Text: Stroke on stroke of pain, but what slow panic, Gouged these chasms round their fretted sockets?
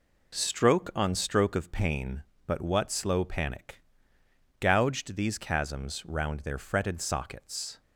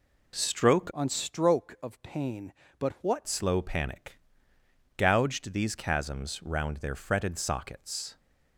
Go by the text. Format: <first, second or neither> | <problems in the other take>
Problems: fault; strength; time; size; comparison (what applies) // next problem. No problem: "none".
first | changes voice from "on" to "what"; from 0.9 to 3.2 s; 2.3 s long